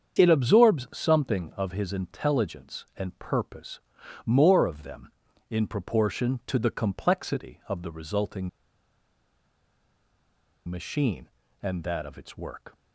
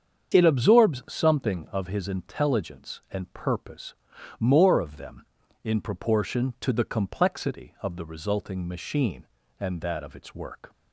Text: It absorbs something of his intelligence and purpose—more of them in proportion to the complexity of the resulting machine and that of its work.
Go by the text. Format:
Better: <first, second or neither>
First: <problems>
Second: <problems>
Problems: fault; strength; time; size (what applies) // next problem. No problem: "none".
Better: second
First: starts louder than the rest; strong; until 1.2 s; 7.5 dB // pauses between "resulting" and "machine"; strong; at 8.4 s; 2.1 s long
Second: starts louder than the rest; strong; until 1.3 s; 7.5 dB